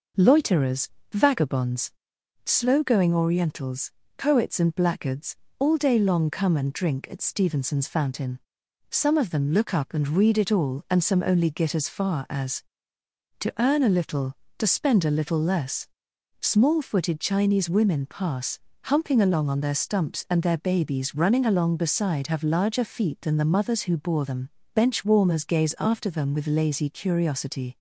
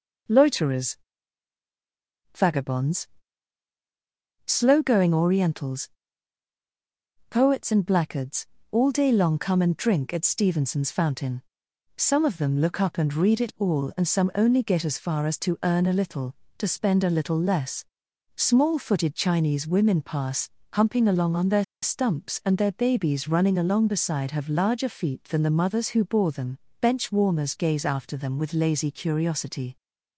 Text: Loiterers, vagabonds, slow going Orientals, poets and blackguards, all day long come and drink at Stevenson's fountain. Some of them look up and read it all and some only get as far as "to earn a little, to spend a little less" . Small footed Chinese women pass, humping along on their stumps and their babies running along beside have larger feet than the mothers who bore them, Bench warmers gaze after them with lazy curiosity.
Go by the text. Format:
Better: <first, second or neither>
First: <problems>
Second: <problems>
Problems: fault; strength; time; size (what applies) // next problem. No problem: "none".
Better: first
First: none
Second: pauses between "their" and "stumps"; slight; at 21.6 s; 0.18 s long